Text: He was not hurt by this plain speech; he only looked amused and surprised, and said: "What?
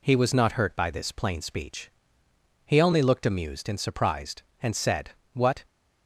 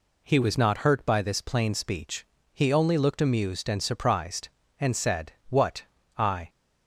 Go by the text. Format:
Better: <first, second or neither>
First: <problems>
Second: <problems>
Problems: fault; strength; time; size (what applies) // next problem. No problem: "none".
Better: first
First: none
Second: goes on to say "I"; slight; from 6.1 s on; 0.32 s long